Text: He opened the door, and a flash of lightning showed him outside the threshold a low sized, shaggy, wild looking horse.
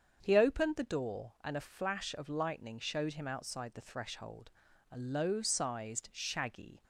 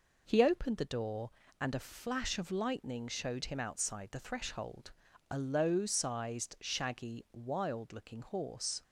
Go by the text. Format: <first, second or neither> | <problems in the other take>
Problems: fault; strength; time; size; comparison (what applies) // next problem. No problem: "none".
second | starts louder than the rest; strong; until 1.2 s; 7 dB // pauses between "threshold" and "a"; at 4.5 s; 0.42 s long; also in the second // stops before "wild looking horse"; at 6.8 s